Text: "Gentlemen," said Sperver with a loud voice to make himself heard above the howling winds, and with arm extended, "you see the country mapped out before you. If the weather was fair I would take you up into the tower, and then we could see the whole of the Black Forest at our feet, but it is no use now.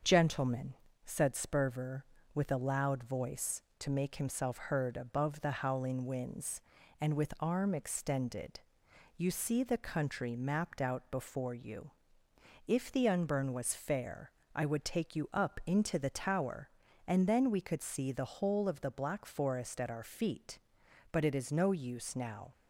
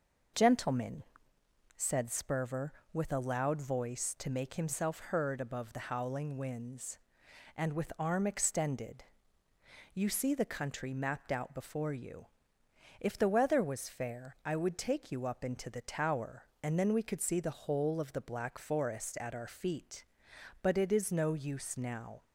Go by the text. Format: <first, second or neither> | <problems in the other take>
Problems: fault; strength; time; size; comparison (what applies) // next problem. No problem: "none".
second | starts louder than the rest; until 1.3 s; 6.5 dB // says "unburn" for "weather"; at 13.0 s // pauses between "fair" and "I"; slight; at 14.3 s; 0.22 s long